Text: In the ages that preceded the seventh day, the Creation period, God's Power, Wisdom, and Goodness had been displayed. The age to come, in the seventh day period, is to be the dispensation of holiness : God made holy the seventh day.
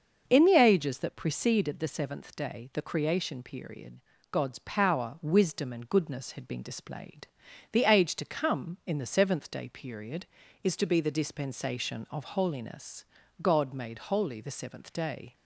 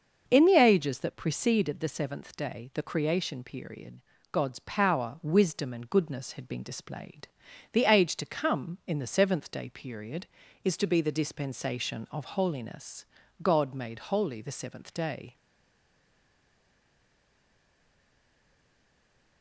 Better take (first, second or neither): first